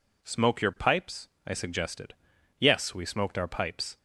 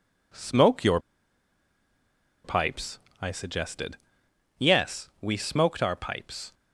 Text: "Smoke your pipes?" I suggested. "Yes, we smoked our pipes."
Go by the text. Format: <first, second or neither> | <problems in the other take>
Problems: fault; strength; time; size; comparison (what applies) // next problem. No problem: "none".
first | pauses between "your" and "pipes"; strong; at 0.9 s; 1.4 s long